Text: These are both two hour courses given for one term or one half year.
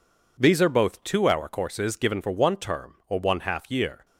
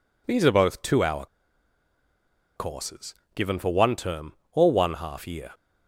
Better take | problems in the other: first | pauses between "hour" and "courses"; strong; at 1.2 s; 1.2 s long // pauses between "courses" and "given"; slight; at 3.1 s; 0.20 s long

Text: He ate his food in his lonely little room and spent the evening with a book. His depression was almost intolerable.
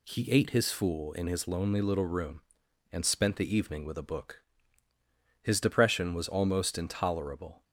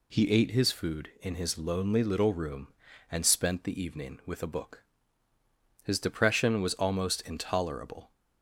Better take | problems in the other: second | says "fool" for "food"; at 0.6 s

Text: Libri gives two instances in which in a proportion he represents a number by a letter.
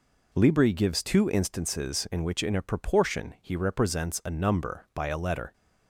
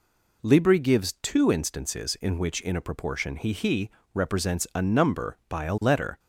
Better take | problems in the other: first | says "he" twice; at 3.5 s

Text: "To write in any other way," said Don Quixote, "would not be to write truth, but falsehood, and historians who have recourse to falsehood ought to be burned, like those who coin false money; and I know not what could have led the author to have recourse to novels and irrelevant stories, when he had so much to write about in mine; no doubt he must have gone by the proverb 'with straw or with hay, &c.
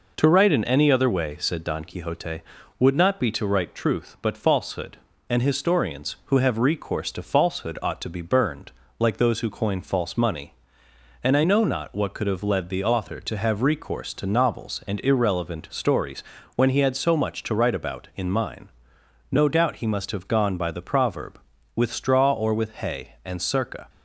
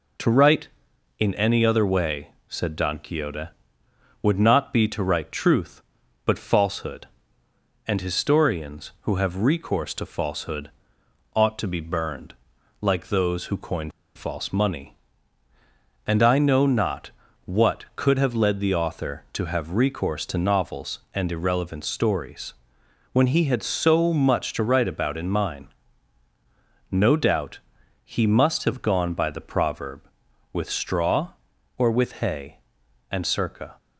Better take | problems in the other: first | pauses between "falsehood" and "ought"; noticeable; at 10.7 s; 0.64 s long // pauses between "coin" and "false"; slight; at 13.9 s; 0.24 s long // pauses between "not" and "what"; slight; at 17.1 s; 0.34 s long // pauses between "doubt" and "he"; noticeable; at 27.5 s; 0.46 s long

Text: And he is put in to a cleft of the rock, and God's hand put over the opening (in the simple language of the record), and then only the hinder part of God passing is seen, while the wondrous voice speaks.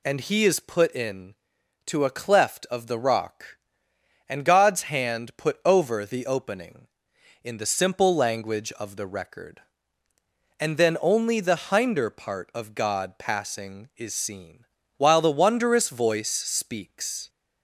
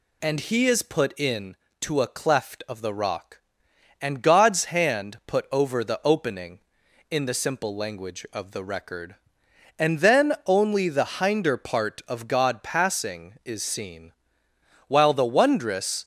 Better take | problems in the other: first | stops before "voice speaks"; at 16.0 s

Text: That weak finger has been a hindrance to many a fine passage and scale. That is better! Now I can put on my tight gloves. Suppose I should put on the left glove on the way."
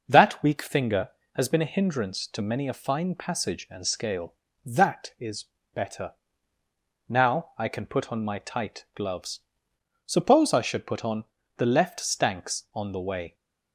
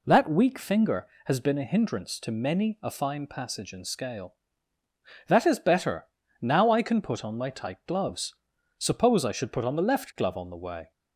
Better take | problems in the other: second | pauses between "is" and "better"; slight; at 5.4 s; 0.30 s long // pauses between "on" and "the"; slight; at 11.2 s; 0.32 s long // says "stanks" for "glove"; at 11.9 s

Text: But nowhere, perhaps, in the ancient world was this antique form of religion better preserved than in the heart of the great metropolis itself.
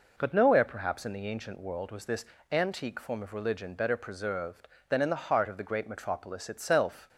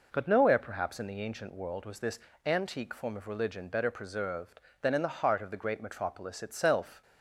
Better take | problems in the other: neither | pauses between "this" and "antique"; slight; the same in both

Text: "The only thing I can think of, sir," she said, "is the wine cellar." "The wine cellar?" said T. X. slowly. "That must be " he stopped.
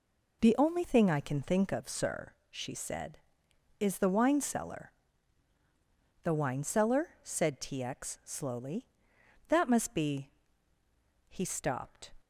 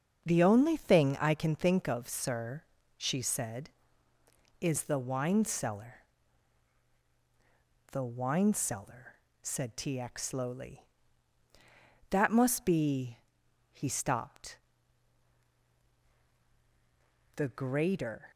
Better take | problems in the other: first | starts louder than the rest; until 1.2 s; 6.5 dB // goes on to say "The greater"; noticeable; from 17.3 s on; 0.94 s long

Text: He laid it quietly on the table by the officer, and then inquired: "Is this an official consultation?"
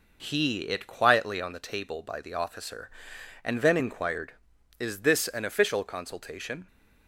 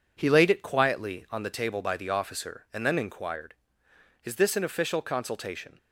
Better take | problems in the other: second | skips "laid"; at 0.6 s

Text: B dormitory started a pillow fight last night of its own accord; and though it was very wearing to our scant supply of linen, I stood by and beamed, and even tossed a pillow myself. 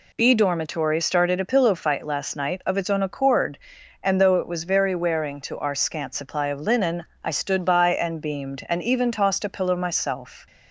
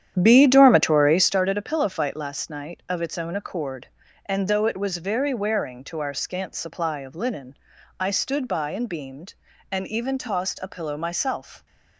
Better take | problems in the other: first | starts louder than the rest; strong; until 1.4 s; 10 dB

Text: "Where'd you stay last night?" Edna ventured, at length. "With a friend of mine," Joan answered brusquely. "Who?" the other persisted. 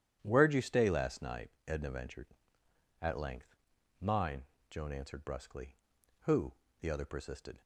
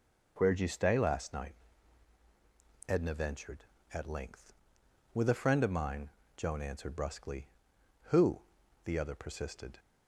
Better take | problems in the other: second | starts louder than the rest; strong; until 1.2 s; 10 dB // skips "With a friend of"; at 3.7 s

